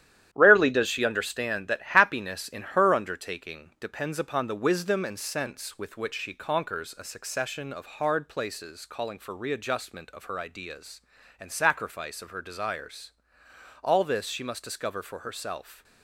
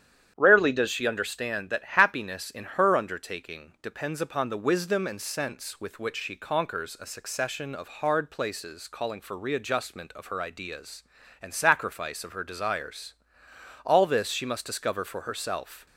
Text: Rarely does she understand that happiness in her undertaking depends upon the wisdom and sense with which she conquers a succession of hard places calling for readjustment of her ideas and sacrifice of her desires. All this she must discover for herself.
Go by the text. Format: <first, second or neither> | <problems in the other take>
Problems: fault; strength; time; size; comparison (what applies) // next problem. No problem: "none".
second | gets quieter; strong; throughout; 7 dB // starts louder than the rest; strong; until 1.3 s; 11 dB; strong in the second